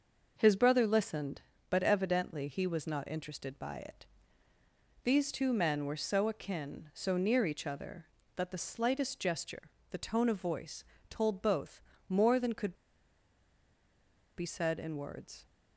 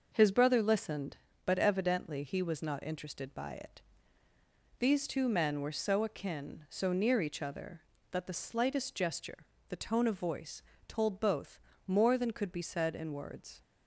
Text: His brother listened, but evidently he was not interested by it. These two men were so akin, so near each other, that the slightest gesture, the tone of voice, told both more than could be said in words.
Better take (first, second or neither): second